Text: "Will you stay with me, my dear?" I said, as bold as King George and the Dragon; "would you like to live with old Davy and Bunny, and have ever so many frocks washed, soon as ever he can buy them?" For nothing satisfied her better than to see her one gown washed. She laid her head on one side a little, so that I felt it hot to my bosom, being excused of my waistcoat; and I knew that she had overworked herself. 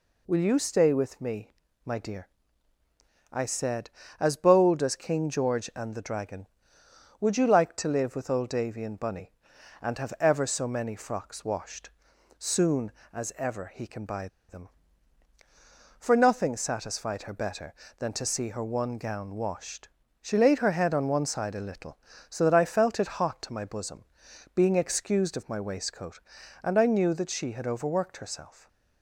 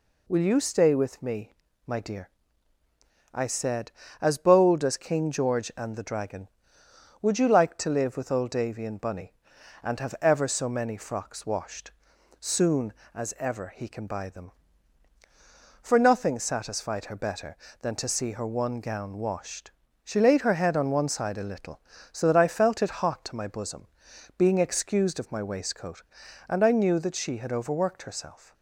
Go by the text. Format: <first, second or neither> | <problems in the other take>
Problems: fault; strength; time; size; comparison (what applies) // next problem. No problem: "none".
second | pauses between "buy" and "them"; slight; at 14.2 s; 0.21 s long // stays silent after the last word; slight; from 28.5 s on; 0.5 s long